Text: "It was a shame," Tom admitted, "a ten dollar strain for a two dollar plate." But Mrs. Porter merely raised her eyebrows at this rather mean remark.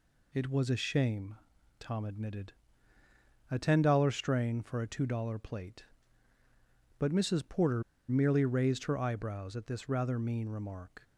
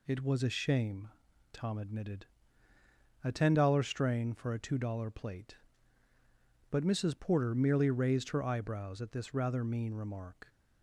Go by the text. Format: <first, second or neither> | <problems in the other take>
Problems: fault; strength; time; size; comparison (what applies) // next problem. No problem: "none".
second | pauses between "Porter" and "merely"; slight; at 7.8 s; 0.26 s long